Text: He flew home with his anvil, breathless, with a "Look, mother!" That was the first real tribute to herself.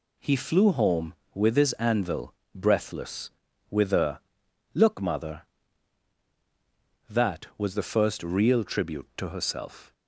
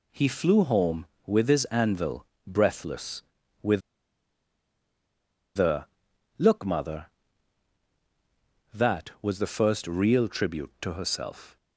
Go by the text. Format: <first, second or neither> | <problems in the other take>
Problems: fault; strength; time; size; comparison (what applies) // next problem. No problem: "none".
first | pauses between "with" and "a"; strong; at 3.8 s; 1.7 s long // pauses between "a" and "Look"; noticeable; at 5.8 s; 0.52 s long; noticeable in the first